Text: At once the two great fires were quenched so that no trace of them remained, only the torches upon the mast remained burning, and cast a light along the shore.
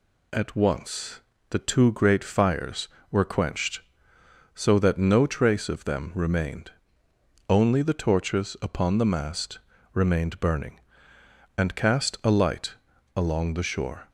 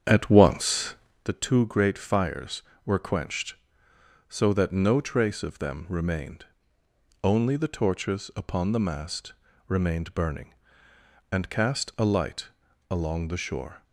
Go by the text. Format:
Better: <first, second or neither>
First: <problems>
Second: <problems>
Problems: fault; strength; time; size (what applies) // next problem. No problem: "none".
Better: first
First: pauses between "once" and "the"; slight; at 1.2 s; 0.30 s long // pauses between "mast" and "remained"; slight; at 9.5 s; 0.34 s long // pauses between "light" and "along"; at 12.7 s; 0.40 s long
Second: starts louder than the rest; strong; until 1.3 s; 8 dB // pauses between "once" and "the"; slight; at 0.9 s; 0.30 s long // pauses between "mast" and "remained"; slight; at 9.3 s; 0.34 s long // pauses between "light" and "along"; at 12.4 s; 0.40 s long